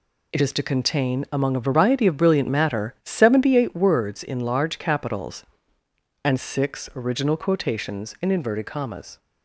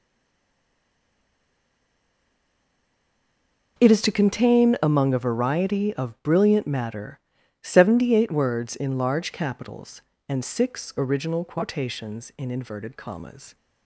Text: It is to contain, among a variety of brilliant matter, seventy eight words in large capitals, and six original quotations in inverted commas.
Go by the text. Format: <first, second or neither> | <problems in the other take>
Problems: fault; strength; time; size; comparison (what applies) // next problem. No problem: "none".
first | stays silent before the first word; strong; until 3.7 s; 3.7 s long